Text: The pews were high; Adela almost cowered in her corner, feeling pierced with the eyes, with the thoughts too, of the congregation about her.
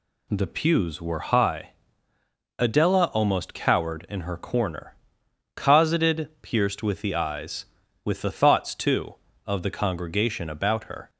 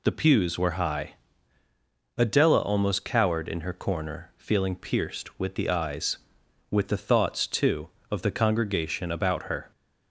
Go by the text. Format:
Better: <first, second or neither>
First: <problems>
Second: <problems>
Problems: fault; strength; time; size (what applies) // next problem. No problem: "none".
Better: second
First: says "cosseted" for "feeling"; at 5.5 s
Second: none